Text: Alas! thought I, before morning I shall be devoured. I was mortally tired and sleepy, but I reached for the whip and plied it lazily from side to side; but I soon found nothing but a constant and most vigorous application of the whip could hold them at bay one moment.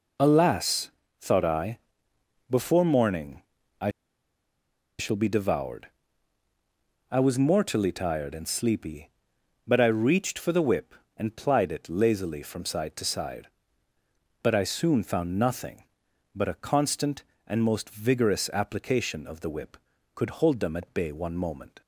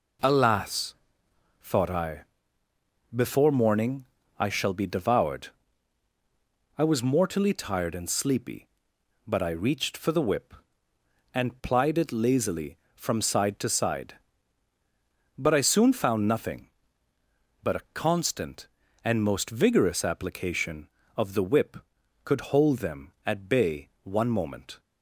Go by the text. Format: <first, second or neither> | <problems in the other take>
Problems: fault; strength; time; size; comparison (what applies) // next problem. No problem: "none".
second | pauses between "morning" and "I"; at 3.4 s; 0.40 s long; slight in the second // pauses between "I" and "shall"; at 3.8 s; 1.0 s long